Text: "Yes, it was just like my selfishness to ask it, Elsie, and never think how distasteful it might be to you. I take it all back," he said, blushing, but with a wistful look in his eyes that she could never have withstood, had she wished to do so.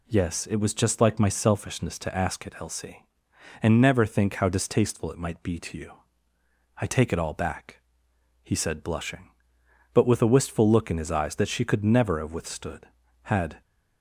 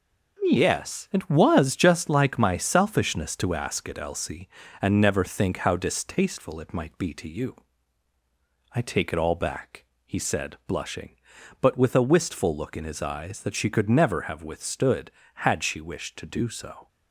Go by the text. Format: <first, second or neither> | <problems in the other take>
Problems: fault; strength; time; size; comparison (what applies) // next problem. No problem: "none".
second | stops before "she wished to do so"; at 13.6 s